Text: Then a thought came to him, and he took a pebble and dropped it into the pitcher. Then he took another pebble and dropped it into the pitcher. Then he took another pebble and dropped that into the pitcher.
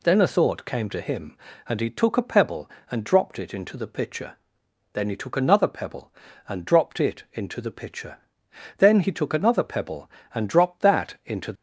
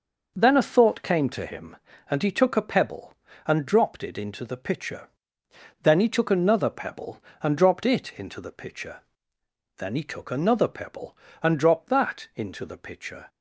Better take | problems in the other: second | stops before "the pitcher"; at 11.5 s

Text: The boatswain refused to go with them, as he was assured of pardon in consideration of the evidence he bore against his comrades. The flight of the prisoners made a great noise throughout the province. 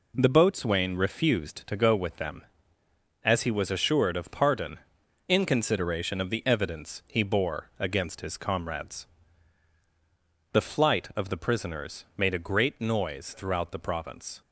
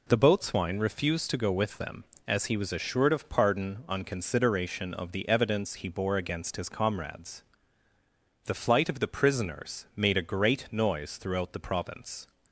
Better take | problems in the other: first | says "on" for "in"; at 3.8 s

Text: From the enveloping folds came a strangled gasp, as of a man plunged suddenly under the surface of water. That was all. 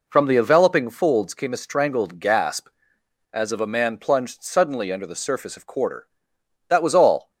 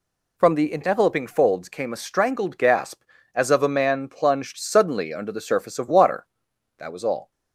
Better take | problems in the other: second | says "quarter" for "water"; at 5.6 s

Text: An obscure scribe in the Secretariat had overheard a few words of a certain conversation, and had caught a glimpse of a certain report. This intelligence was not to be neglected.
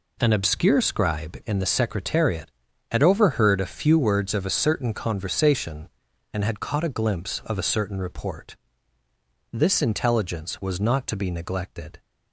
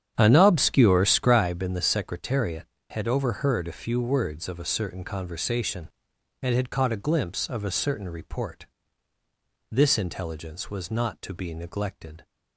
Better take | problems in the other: first | starts louder than the rest; strong; until 1.5 s; 9 dB

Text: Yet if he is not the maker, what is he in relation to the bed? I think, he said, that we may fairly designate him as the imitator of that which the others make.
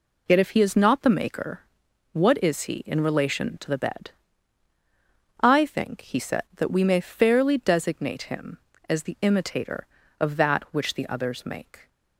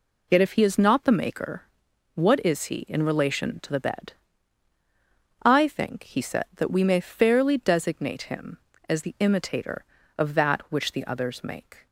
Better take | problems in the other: neither | none

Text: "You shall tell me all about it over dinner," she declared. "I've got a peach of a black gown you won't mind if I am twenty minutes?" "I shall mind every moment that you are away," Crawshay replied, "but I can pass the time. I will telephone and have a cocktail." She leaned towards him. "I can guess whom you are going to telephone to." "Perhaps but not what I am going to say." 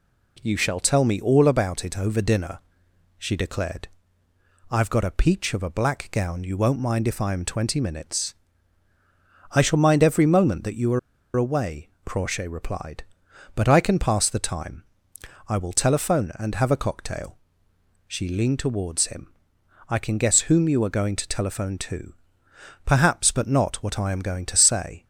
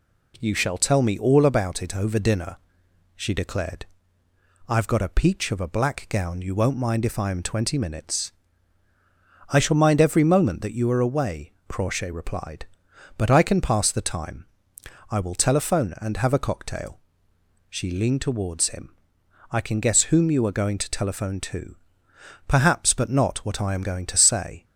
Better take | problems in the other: second | pauses between "are" and "away"; at 10.9 s; 0.36 s long

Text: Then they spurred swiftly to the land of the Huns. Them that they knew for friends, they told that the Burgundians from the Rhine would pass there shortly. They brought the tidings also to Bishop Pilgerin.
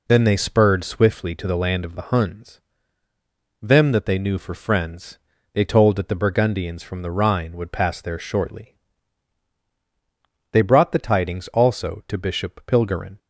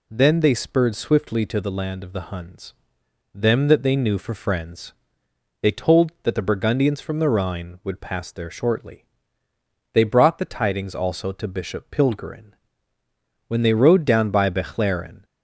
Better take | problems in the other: first | goes on to say "When they rode down by Bechlaren"; strong; from 13.4 s on; 1.7 s long

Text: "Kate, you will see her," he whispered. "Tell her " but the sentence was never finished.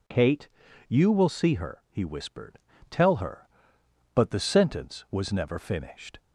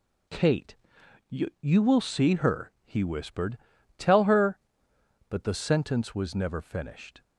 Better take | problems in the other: first | says "you" twice; at 1.6 s

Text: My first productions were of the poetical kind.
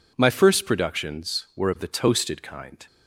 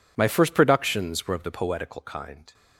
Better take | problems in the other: second | says "toasted" for "poetical"; at 1.8 s

